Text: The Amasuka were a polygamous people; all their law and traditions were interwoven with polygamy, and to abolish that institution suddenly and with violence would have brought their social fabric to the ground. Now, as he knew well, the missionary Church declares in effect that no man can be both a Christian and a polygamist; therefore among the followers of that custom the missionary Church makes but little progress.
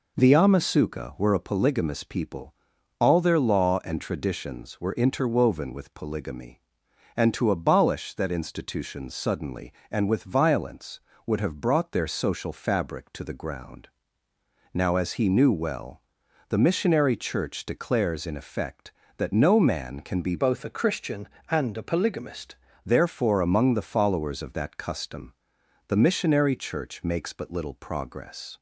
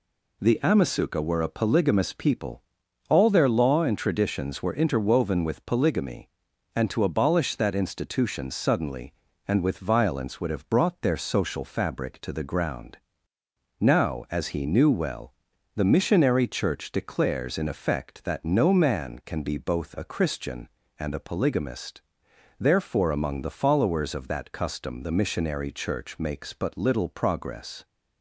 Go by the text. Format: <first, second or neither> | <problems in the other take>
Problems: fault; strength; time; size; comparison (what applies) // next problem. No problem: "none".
second | changes voice from "both" to "polygamist"; from 20.3 to 22.5 s; 2.2 s long // pauses between "custom" and "the"; noticeable; at 25.3 s; 0.54 s long